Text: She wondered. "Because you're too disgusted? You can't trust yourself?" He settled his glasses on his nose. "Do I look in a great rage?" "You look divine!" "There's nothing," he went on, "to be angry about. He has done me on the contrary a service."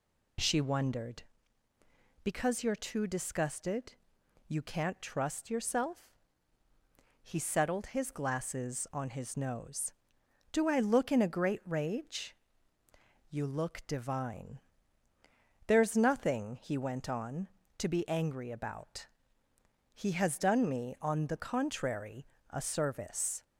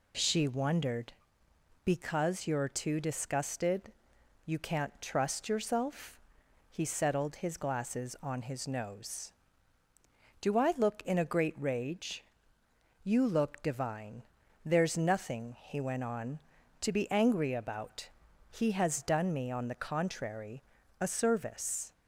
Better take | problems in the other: neither | pauses between "contrary" and "a"; slight; the same in both

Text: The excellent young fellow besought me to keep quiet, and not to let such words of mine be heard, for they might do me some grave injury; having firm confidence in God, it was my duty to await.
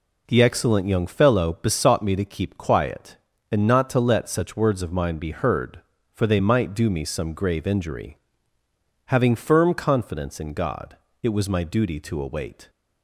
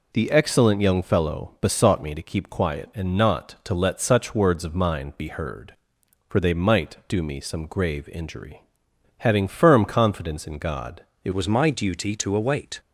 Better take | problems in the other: first | changes voice at "was"; from 11.3 s on; 1.4 s long

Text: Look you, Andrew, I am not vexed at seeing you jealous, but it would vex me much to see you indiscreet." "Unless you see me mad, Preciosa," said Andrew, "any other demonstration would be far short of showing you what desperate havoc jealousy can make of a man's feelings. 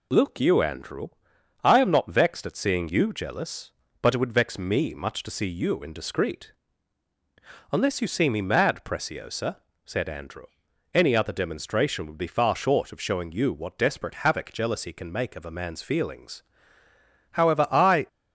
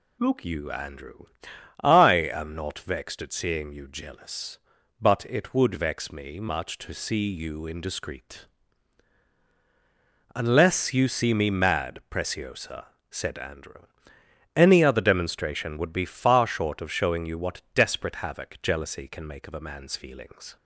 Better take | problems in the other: second | goes on to say "However I"; noticeable; from 17.3 s on; 0.74 s long

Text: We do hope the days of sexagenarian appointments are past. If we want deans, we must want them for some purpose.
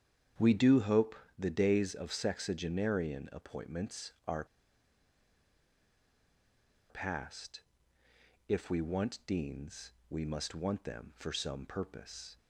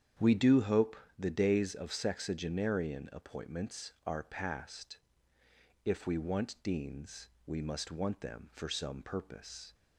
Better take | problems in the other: second | starts louder than the rest; strong; until 1.6 s; 8.5 dB; strong in the second // pauses between "hope" and "the"; slight; at 1.1 s; 0.24 s long; slight in the second // pauses between "are" and "past"; strong; at 4.4 s; 2.4 s long

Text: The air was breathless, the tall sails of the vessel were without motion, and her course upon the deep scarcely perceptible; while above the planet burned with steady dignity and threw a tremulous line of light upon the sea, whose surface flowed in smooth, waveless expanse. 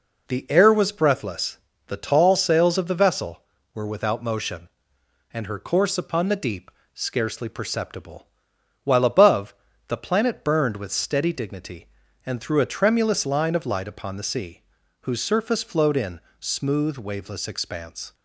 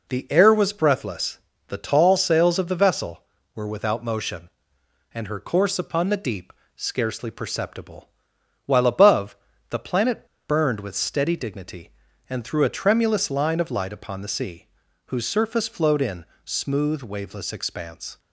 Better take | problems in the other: first | pauses between "deep" and "scarcely"; slight; at 6.5 s; 0.24 s long; slight in the first // pauses between "above" and "the"; slight; at 9.3 s; 0.34 s long; slight in the first // pauses between "planet" and "burned"; slight; at 10.2 s; 0.24 s long // pauses between "in" and "smooth"; slight; at 16.2 s; 0.18 s long; slight in the first

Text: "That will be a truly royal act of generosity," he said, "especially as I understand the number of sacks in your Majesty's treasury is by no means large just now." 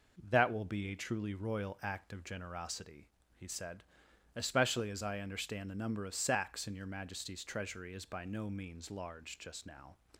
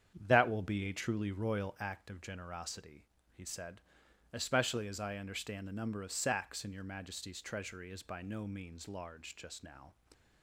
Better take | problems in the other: first | starts louder than the rest; strong; until 1.9 s; 8.5 dB

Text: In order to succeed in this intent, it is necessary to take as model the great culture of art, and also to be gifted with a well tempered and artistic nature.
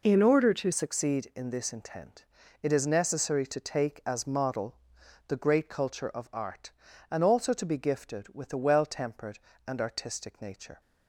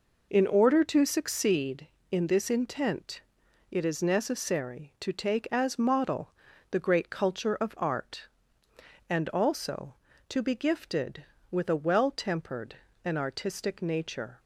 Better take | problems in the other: second | changes voice at "succeed"; from 0.7 s on; 10.1 s long // pauses between "model" and "the"; noticeable; at 4.7 s; 0.54 s long; also in the second

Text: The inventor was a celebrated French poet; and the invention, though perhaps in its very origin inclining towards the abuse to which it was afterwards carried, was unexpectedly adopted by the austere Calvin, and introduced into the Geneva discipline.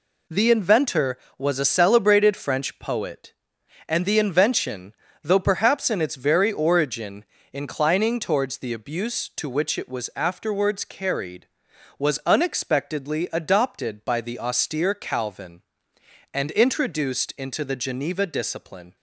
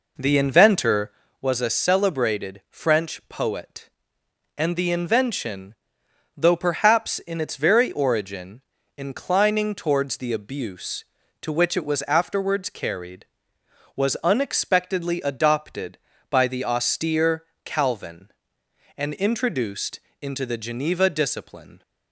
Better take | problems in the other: first | starts louder than the rest; noticeable; until 1.3 s; 4.5 dB // pauses between "origin" and "inclining"; slight; at 8.6 s; 0.34 s long; slight in the first // pauses between "austere" and "Calvin"; slight; at 17.4 s; 0.22 s long // pauses between "introduced" and "into"; slight; at 19.9 s; 0.22 s long

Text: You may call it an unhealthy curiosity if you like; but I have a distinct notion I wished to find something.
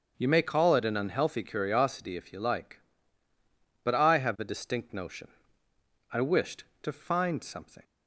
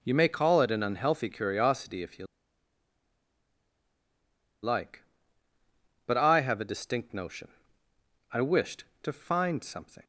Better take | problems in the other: first | starts louder than the rest; until 1.0 s; 6.5 dB; also in the first // pauses between "you" and "like"; strong; at 2.2 s; 2.3 s long // pauses between "notion" and "I"; noticeable; at 7.4 s; 0.84 s long; noticeable in the first

